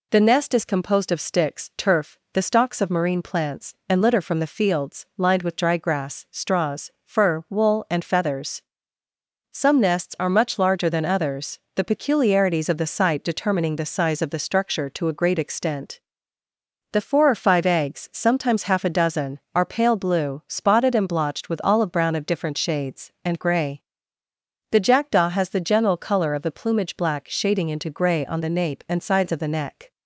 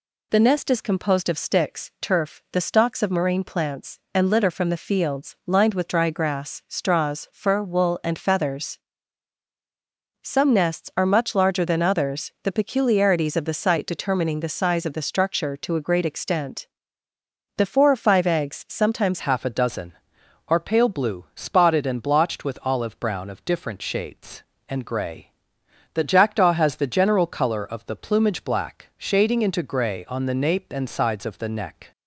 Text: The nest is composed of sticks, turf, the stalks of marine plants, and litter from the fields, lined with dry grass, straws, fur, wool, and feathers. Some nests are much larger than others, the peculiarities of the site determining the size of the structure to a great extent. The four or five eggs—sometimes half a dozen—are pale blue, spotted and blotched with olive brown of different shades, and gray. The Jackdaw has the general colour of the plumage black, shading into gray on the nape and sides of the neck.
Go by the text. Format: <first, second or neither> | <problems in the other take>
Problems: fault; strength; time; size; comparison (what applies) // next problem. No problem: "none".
first | changes voice at "half"; from 19.1 s on; 12.8 s long